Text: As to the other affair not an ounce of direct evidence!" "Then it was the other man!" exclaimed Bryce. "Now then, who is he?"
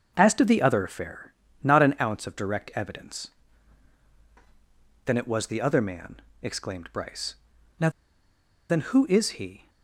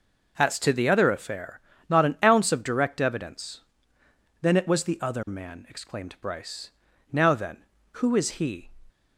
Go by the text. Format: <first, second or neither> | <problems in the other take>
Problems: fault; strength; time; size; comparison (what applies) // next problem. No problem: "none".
second | starts louder than the rest; until 1.1 s; 6.5 dB // pauses between "affair" and "not"; slight; at 1.3 s; 0.34 s long; slight in the second // pauses between "Now" and "then"; noticeable; at 7.8 s; 0.80 s long